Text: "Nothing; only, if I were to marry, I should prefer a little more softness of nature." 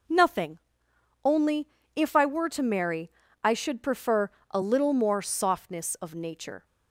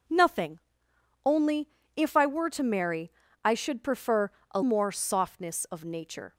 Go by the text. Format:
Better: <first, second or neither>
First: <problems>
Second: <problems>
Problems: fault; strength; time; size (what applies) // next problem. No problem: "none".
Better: first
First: pauses between "prefer" and "a"; slight; at 4.2 s; 0.22 s long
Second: pauses between "prefer" and "a"; slight; at 4.3 s; 0.22 s long // skips "little"; at 4.6 s